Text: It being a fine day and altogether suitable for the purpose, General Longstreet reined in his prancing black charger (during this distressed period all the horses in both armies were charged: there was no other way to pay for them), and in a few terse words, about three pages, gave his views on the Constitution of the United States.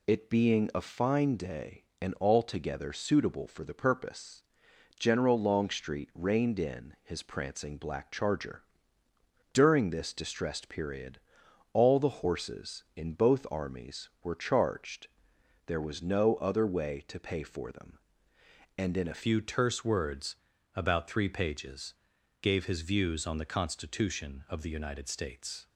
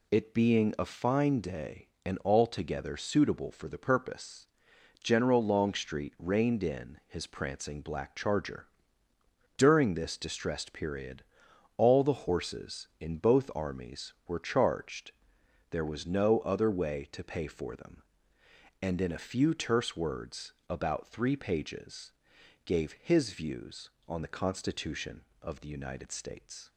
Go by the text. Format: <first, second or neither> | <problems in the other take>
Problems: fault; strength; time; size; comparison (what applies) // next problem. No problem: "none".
second | pauses between "period" and "all"; noticeable; at 11.1 s; 0.54 s long; noticeable in the second // changes voice at "few"; from 19.2 s on; 6.4 s long